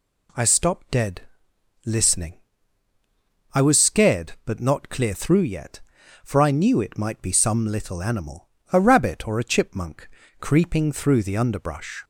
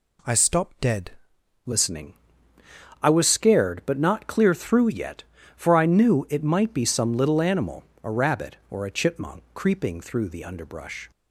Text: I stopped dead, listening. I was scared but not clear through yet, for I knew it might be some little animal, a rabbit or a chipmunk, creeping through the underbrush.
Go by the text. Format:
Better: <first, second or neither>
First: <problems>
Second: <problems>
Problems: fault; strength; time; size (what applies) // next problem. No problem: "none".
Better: first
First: none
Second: changes voice at "listening"; from 1.6 s on; 9.5 s long